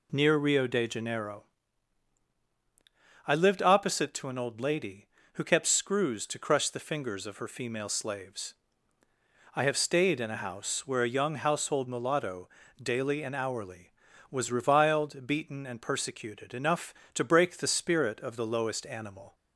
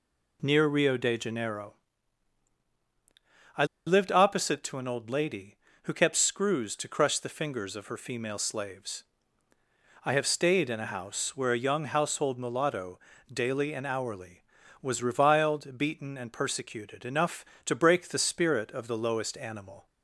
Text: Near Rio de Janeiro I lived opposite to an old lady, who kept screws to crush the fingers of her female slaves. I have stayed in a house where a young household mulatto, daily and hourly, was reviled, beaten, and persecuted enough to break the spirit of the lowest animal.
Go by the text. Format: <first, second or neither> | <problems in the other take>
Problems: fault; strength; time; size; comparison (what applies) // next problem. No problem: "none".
first | pauses between "Janeiro" and "I"; strong; at 1.7 s; 1.8 s long; strong in the first // pauses between "I" and "lived"; slight; at 3.6 s; 0.21 s long